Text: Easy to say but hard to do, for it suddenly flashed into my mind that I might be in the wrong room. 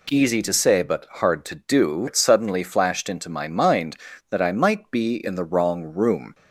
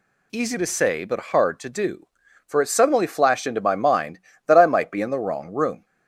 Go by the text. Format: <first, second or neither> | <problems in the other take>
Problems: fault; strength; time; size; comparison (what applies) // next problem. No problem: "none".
second | skips "for"; at 2.0 s